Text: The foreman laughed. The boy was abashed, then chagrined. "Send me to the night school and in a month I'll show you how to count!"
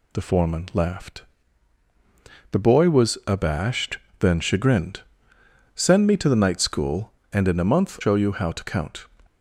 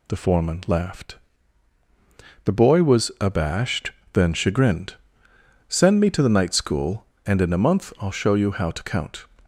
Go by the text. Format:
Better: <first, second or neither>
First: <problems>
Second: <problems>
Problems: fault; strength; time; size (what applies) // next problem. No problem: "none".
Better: second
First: skips "I'll"; at 7.9 s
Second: none